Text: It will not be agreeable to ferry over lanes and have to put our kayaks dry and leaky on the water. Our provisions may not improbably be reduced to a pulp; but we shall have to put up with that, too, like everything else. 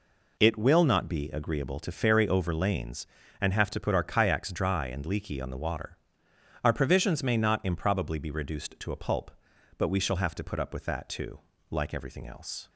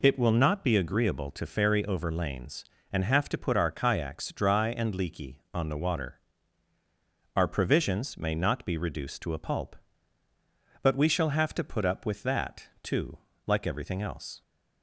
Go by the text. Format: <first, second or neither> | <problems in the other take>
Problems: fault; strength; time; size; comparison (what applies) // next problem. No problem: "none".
first | skips "improbably"; at 8.6 s